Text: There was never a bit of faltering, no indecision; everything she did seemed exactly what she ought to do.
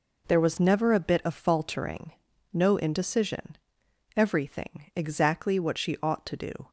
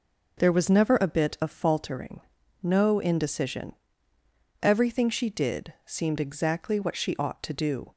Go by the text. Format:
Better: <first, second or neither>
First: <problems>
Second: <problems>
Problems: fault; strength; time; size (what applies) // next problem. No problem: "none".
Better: second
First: skips "she did seemed"; at 4.9 s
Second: none